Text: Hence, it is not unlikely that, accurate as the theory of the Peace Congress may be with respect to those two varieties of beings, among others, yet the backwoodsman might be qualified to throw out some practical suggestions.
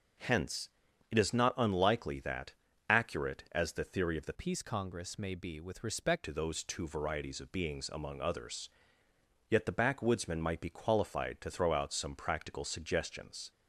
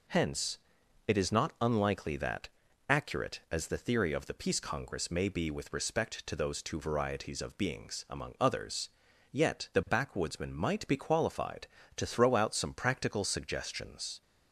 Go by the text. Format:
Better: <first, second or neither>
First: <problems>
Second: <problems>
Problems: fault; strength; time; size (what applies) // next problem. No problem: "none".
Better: second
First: changes voice from "Peace" to "respect"; from 4.3 to 6.2 s; 1.9 s long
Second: none